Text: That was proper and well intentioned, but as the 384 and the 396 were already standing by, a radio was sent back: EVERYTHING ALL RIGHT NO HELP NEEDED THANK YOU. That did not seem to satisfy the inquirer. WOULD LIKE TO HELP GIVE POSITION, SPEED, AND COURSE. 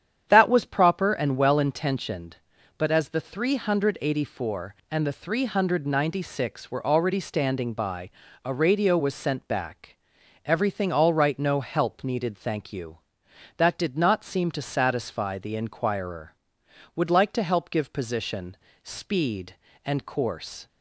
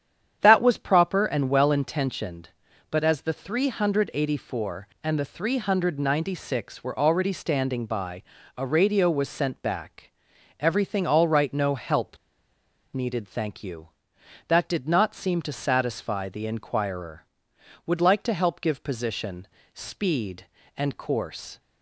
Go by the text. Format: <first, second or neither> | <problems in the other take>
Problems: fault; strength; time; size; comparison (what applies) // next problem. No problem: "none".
first | starts louder than the rest; strong; until 1.4 s; 9 dB; strong in the first // pauses between "HELP" and "NEEDED"; noticeable; at 12.1 s; 0.76 s long